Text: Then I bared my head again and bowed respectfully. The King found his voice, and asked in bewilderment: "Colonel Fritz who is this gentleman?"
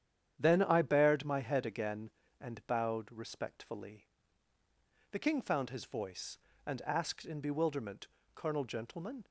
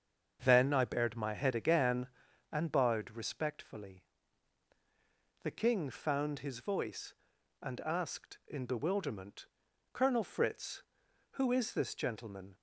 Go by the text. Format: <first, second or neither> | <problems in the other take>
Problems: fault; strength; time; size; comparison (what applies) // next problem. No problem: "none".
second | starts louder than the rest; strong; until 1.4 s; 9.5 dB; also in the second // skips "Fritz who is this"; at 8.6 s